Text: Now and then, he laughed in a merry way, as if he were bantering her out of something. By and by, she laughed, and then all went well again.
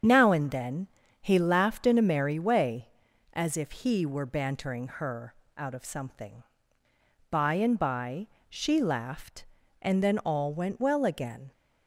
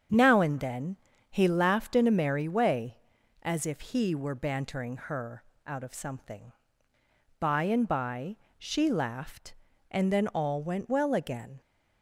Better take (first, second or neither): second